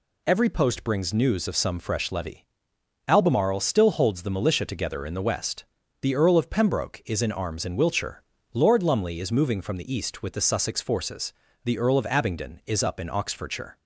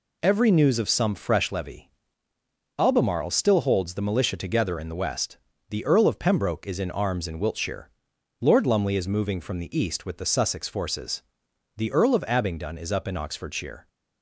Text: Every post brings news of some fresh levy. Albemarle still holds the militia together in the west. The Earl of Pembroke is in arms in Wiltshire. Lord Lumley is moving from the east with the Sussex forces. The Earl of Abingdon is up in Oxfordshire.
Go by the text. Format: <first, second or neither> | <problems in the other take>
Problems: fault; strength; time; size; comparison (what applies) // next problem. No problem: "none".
first | skips "post brings"; at 0.5 s